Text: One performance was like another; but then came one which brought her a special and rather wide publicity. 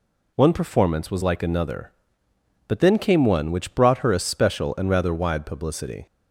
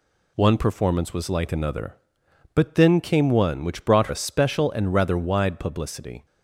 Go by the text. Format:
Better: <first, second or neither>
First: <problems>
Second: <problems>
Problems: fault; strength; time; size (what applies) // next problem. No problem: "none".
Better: first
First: none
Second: skips "her"; at 4.0 s